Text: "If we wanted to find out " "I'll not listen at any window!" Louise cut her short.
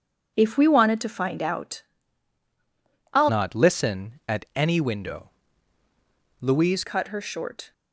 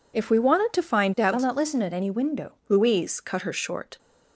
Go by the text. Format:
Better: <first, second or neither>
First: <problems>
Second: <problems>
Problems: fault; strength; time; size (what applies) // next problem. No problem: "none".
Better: second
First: starts louder than the rest; until 1.3 s; 7 dB // changes voice from "not" to "Louise"; from 3.2 to 6.8 s; 3.6 s long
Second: none